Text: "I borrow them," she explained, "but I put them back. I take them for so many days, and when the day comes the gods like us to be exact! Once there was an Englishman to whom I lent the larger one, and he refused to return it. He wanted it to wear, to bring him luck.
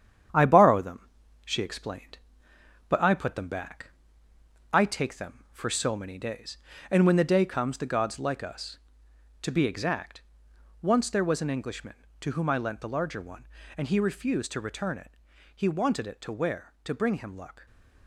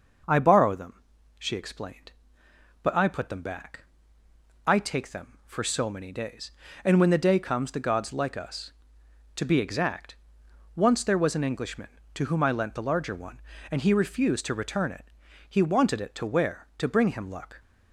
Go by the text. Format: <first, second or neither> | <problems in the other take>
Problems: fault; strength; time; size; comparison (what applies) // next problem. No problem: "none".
second | gets quieter; throughout; 3.5 dB // starts louder than the rest; strong; until 1.6 s; 9 dB; noticeable in the second // stays silent after the last word; slight; from 17.5 s on; 0.5 s long